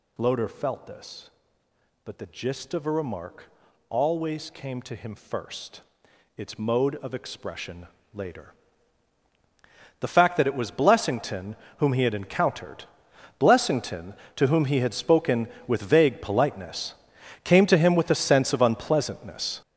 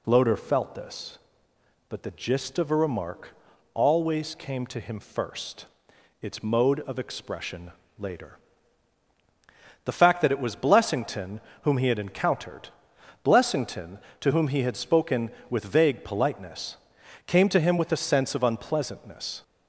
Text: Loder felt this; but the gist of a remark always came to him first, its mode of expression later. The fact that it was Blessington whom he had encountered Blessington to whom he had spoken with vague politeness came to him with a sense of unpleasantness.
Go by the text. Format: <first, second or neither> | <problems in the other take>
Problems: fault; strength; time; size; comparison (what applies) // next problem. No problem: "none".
second | gets louder; strong; throughout; 11 dB // pauses between "remark" and "always"; at 3.4 s; 0.40 s long; also in the second // pauses between "expression" and "later"; slight; at 7.8 s; 0.26 s long; slight in the second // pauses between "Blessington" and "whom"; slight; at 11.5 s; 0.22 s long; slight in the second // pauses between "encountered" and "Blessington"; noticeable; at 12.8 s; 0.54 s long; noticeable in the second // pauses between "politeness" and "came"; noticeable; at 16.9 s; 0.50 s long; noticeable in the second